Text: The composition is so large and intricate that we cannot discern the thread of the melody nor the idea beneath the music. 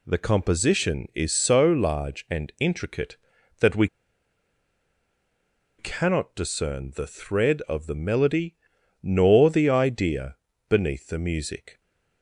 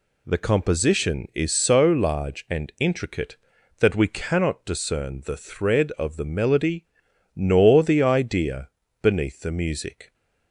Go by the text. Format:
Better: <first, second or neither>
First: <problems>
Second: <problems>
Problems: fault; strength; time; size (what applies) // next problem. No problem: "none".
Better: second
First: pauses between "we" and "cannot"; strong; at 3.8 s; 1.9 s long // pauses between "melody" and "nor"; noticeable; at 8.5 s; 0.48 s long // pauses between "idea" and "beneath"; slight; at 10.3 s; 0.32 s long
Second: pauses between "melody" and "nor"; noticeable; at 6.8 s; 0.51 s long // pauses between "idea" and "beneath"; slight; at 8.6 s; 0.32 s long